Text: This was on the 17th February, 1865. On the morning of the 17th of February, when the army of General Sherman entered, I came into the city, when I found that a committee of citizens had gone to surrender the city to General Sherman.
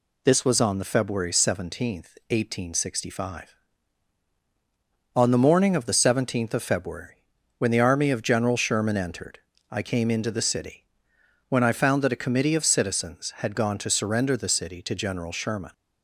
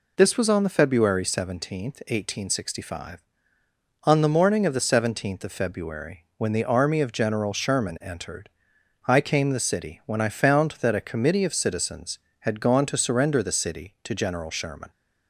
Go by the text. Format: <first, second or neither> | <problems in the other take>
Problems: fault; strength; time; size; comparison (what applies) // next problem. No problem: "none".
first | skips "into"; at 9.5 s